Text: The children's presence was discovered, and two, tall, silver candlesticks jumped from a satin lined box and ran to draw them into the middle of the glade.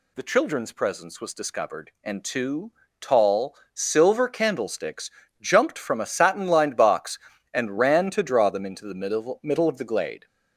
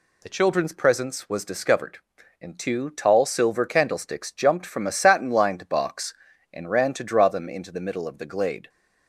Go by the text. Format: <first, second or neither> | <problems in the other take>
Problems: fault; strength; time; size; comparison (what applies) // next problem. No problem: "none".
second | pauses between "candlesticks" and "jumped"; slight; at 5.0 s; 0.32 s long // says "middle" twice; at 9.4 s